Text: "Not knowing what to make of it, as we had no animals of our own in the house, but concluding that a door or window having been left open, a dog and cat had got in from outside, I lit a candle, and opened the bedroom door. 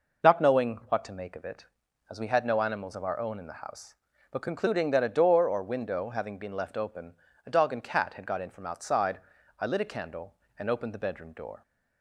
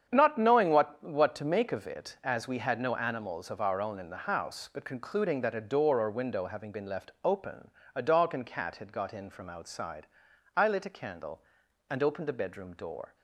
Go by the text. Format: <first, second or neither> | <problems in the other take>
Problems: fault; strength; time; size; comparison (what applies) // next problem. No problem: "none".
first | starts louder than the rest; strong; until 1.1 s; 8 dB // says "what" twice; at 1.0 s